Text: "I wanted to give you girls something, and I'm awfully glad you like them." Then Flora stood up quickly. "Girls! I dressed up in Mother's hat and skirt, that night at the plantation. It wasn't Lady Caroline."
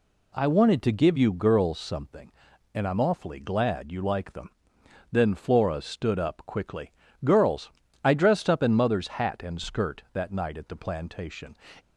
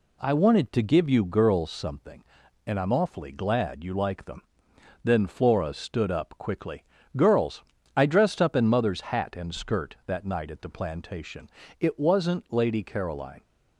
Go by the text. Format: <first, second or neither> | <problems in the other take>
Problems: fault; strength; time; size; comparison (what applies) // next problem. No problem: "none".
second | stops before "It wasn't Lady Caroline"; at 11.7 s